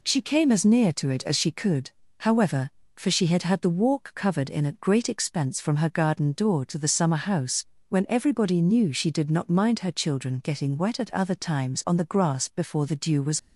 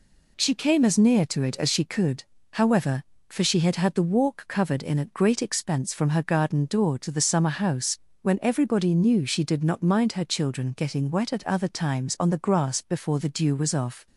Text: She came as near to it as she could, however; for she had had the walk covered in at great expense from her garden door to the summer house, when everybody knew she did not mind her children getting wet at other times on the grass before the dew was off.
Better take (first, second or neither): second